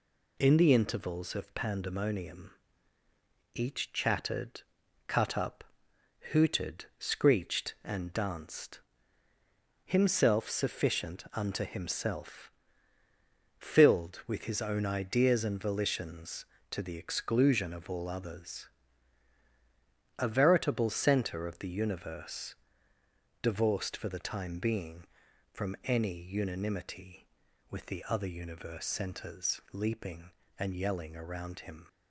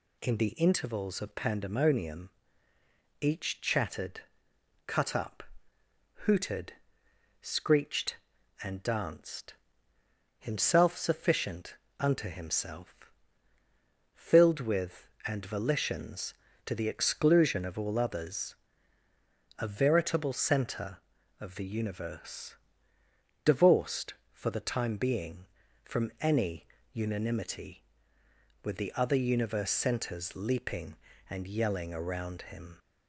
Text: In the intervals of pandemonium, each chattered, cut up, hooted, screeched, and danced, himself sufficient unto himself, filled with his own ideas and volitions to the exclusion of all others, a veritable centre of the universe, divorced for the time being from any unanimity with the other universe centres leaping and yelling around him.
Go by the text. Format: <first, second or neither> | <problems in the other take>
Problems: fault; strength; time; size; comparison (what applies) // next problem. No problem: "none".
first | pauses between "sufficient" and "unto"; slight; at 11.7 s; 0.24 s long // skips "his own ideas"; at 15.1 s // pauses between "any" and "unanimity"; slight; at 26.6 s; 0.26 s long